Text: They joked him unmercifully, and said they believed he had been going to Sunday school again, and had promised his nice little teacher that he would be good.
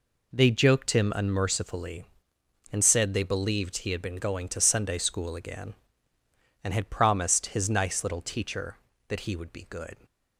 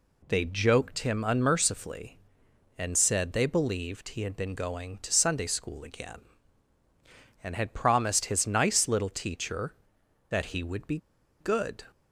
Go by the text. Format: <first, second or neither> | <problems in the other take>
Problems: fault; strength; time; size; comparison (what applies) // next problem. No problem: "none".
first | pauses between "be" and "good"; at 10.9 s; 0.43 s long